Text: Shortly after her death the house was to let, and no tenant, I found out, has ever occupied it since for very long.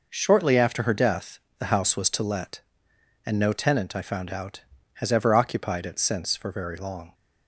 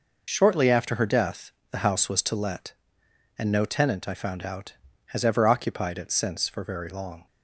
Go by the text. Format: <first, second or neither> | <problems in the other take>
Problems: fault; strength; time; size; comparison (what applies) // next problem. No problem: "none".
first | loses the start of "Shortly"; at 0.2 s; 60 ms // pauses between "death" and "the"; slight; at 1.5 s; 0.20 s long; slight in the first